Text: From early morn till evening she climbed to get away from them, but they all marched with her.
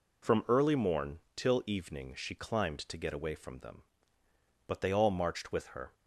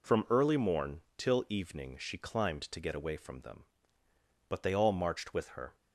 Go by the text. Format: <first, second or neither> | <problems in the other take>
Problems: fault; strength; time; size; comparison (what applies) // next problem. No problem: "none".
neither | pauses between "morn" and "till"; slight; the same in both